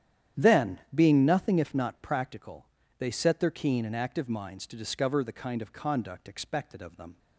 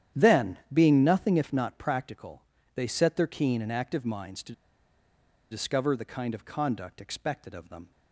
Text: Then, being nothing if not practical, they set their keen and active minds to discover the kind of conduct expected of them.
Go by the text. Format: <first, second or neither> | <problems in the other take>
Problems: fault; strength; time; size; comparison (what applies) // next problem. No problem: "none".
first | starts louder than the rest; strong; until 1.3 s; 10 dB; strong in the first // pauses between "to" and "discover"; at 4.5 s; 0.98 s long